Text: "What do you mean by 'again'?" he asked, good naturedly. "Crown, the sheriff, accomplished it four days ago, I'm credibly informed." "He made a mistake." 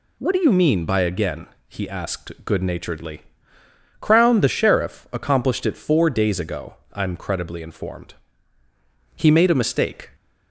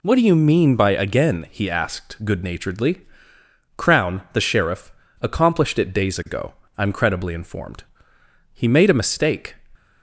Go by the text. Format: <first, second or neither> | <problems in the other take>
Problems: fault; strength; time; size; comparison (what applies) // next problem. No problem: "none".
first | skips "four"; at 5.9 s